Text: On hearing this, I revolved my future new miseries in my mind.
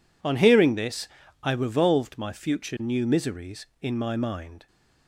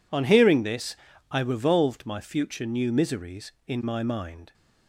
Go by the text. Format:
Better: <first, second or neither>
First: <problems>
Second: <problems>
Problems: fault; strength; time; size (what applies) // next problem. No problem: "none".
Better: neither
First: none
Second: none